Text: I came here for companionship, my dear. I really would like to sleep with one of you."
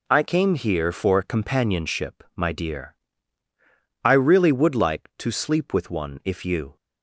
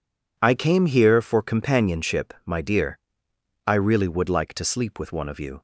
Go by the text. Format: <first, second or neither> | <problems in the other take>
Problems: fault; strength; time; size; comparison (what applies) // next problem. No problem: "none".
second | says "if" for "of"; at 6.2 s